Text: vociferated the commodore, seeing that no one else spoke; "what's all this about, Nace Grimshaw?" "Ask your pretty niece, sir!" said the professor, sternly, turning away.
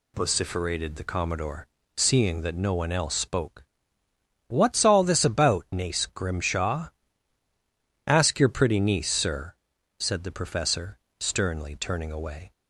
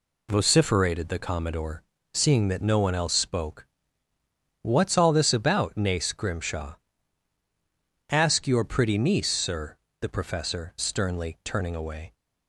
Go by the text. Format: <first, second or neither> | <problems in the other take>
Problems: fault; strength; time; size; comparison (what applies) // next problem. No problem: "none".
first | skips "said"; at 9.8 s